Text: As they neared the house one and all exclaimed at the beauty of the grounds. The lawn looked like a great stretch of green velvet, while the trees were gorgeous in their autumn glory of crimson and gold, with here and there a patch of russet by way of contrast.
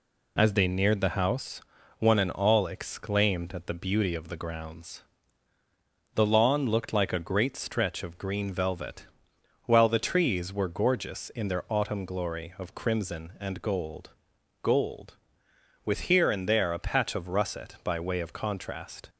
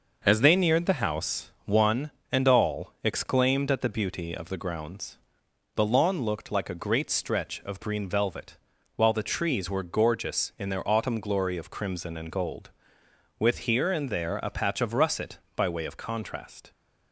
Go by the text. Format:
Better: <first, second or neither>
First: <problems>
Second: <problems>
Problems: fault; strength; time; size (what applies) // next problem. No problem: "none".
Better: second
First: pauses between "house" and "one"; slight; at 1.6 s; 0.36 s long // says "gold" twice; at 14.6 s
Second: none